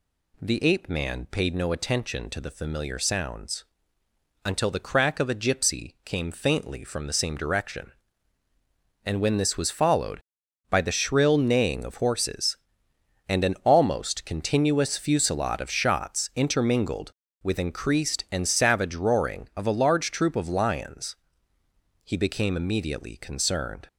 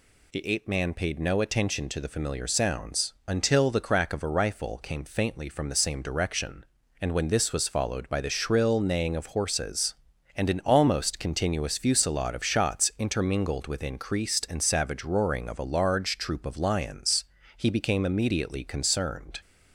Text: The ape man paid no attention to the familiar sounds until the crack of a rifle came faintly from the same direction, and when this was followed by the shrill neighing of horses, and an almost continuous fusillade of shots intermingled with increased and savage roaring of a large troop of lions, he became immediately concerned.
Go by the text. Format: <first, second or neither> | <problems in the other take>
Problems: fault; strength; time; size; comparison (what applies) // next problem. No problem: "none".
second | pauses between "sounds" and "until"; noticeable; at 3.6 s; 0.84 s long; slight in the second // says "gypsy" for "rifle"; at 5.3 s